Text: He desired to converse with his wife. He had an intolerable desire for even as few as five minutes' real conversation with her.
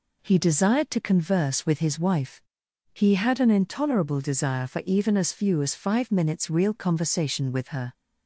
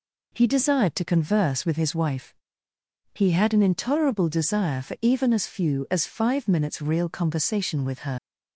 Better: first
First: none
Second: leaves "her" unfinished; at 8.1 s; 70 ms

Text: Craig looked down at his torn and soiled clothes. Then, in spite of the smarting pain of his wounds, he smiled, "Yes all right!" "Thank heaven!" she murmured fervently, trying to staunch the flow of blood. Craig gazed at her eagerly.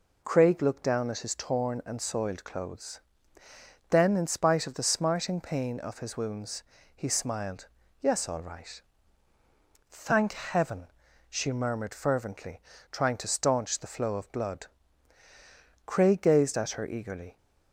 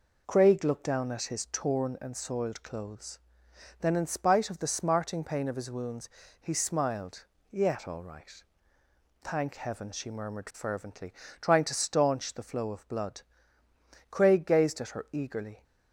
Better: first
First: none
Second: says "Yet" for "Yes"; at 7.5 s

